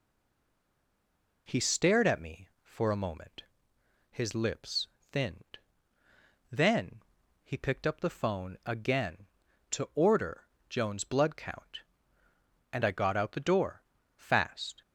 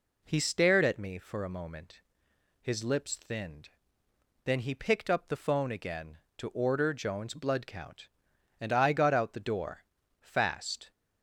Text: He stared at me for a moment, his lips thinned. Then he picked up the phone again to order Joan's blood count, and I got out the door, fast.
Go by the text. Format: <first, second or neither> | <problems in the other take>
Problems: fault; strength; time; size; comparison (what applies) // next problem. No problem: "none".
second | stays silent before the first word; noticeable; until 1.4 s; 1.4 s long // pauses between "lips" and "thinned"; slight; at 4.8 s; 0.24 s long // pauses between "Then" and "he"; at 7.0 s; 0.40 s long // pauses between "order" and "Joan's"; slight; at 10.4 s; 0.24 s long